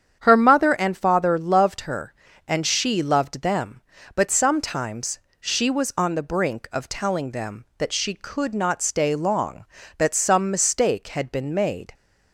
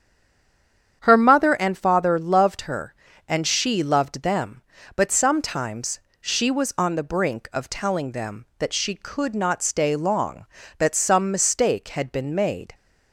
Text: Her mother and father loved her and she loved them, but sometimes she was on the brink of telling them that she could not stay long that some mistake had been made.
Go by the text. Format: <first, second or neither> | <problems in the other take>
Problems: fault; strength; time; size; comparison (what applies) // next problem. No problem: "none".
first | stays silent before the first word; until 1.0 s; 1.0 s long // starts louder than the rest; strong; until 2.0 s; 8.5 dB; strong in the first // pauses between "sometimes" and "she"; slight; at 5.9 s; 0.22 s long; slight in the first